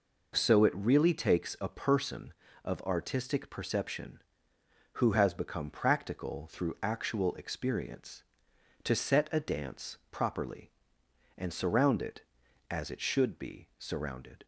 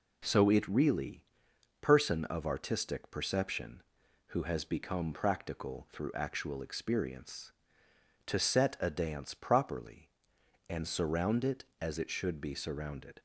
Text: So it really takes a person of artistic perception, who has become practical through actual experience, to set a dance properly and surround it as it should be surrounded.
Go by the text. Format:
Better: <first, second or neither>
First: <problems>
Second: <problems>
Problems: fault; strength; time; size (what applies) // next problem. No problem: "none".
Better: first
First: none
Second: skips "takes a"; at 1.5 s